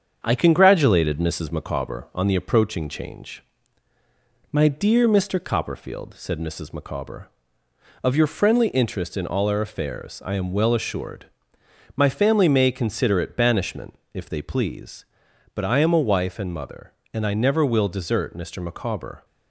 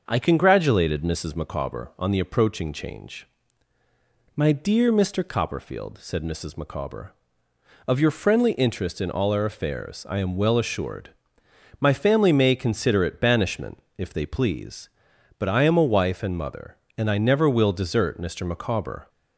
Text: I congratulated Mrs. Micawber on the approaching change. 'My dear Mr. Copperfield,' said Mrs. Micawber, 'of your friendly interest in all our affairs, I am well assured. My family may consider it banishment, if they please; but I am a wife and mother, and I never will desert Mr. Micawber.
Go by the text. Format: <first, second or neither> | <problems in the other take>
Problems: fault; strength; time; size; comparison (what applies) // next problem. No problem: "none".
second | gets quieter; slight; throughout; 3 dB // starts louder than the rest; strong; until 1.2 s; 7.5 dB; also in the second